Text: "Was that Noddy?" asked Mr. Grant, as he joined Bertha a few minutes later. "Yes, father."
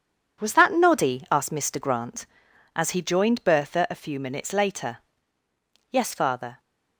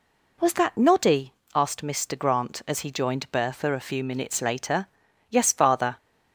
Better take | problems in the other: second | gets quieter; strong; throughout; 8 dB

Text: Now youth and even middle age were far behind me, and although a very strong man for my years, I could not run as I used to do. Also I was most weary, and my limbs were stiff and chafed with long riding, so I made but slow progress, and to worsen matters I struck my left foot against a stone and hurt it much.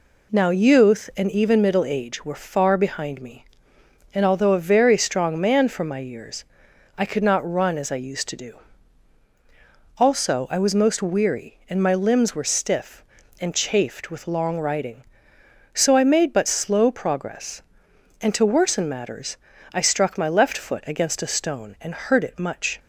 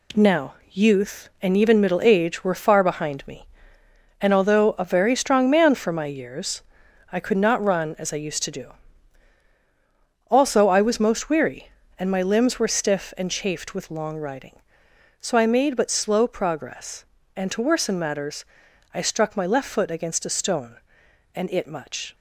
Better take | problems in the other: first | pauses between "Now" and "youth"; slight; at 0.5 s; 0.16 s long // pauses between "matters" and "I"; noticeable; at 18.4 s; 0.50 s long; also in the first // skips "hurt"; at 21.5 s

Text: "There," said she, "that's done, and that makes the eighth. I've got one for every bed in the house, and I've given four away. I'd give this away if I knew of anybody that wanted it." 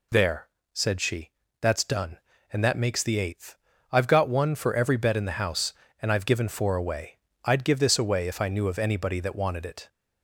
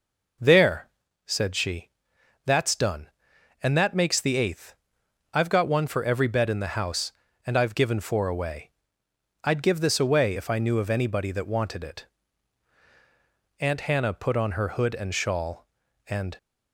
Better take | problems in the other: first | goes on to say "Aunt Hannah put on her hood and shawl and"; strong; from 13.6 s on; 2.7 s long

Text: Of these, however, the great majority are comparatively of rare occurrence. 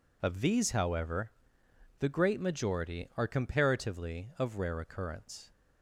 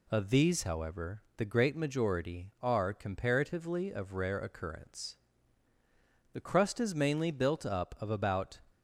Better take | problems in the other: first | goes on to say "The crust is mainly built up of about"; strong; from 6.3 s on; 2.2 s long

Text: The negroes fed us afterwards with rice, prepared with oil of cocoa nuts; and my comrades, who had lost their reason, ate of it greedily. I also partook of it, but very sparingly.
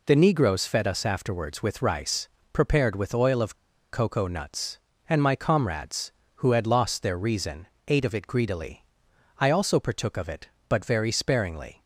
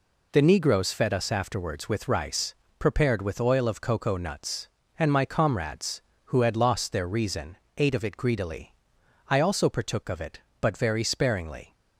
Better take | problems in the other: second | pauses between "of" and "cocoa"; at 3.5 s; 0.37 s long

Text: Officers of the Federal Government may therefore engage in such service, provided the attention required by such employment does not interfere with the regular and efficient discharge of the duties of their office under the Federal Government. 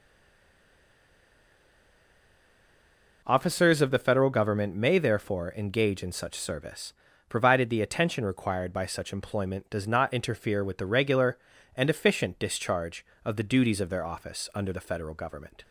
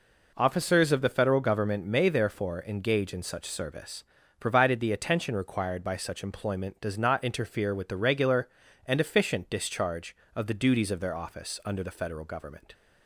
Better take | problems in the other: second | stays silent before the first word; strong; until 3.2 s; 3.2 s long

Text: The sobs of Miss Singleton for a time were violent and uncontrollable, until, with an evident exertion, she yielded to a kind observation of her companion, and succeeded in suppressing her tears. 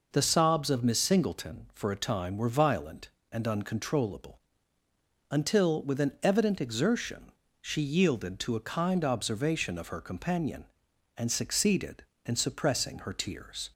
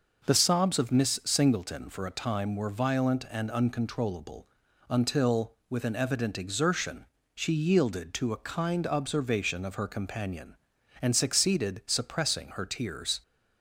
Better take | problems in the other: first | starts louder than the rest; noticeable; until 1.3 s; 6 dB // skips "in"; at 11.8 s

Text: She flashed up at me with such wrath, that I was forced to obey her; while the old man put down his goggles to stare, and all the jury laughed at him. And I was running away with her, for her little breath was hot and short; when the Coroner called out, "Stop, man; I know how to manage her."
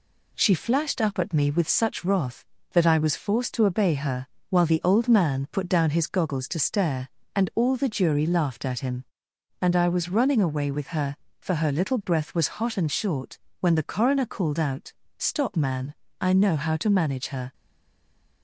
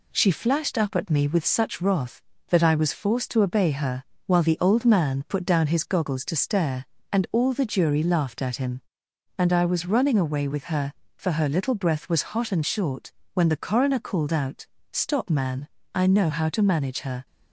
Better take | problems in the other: second | stays silent after the last word; slight; from 17.5 s on; 0.9 s long

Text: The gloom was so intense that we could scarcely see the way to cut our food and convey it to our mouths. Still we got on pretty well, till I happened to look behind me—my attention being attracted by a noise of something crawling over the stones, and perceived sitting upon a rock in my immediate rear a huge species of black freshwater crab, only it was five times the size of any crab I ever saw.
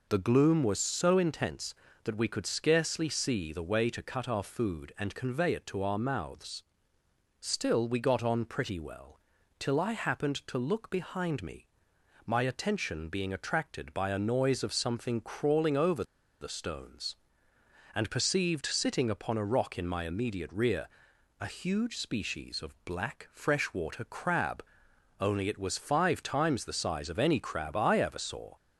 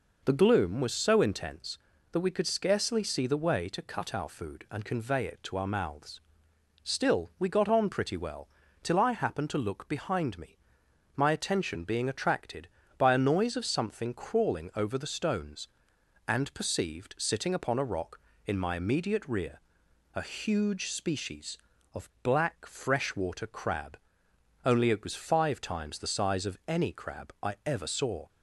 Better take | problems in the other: second | pauses between "over" and "the"; at 16.0 s; 0.37 s long // pauses between "rear" and "a"; noticeable; at 20.8 s; 0.52 s long; noticeable in the second

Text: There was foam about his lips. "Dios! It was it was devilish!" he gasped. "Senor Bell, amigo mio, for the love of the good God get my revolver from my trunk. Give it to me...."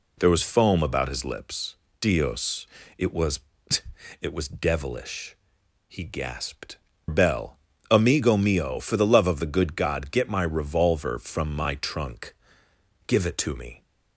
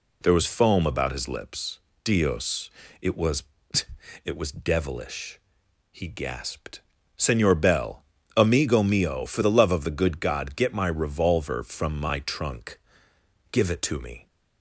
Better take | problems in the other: second | pauses between "was" and "it"; noticeable; at 3.3 s; 0.82 s long; noticeable in the second // skips "Senor"; at 6.9 s

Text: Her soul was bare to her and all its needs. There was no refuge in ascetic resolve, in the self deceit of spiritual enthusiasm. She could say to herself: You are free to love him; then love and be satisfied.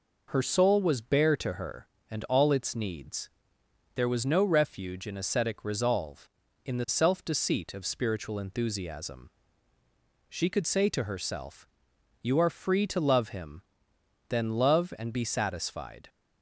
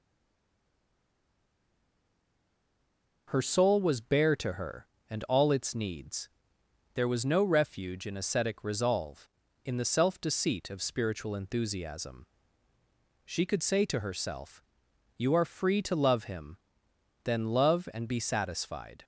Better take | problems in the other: first | stays silent before the first word; strong; until 3.2 s; 3.2 s long

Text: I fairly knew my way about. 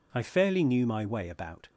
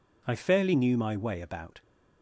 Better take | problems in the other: neither | none

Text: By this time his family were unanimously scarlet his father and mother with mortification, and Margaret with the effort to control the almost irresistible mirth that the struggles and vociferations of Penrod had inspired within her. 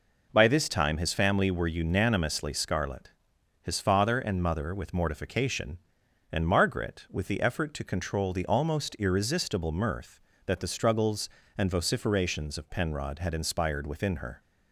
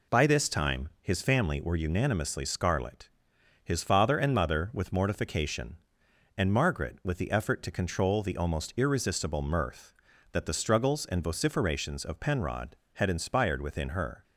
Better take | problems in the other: neither | pauses between "scarlet" and "his"; noticeable; the same in both

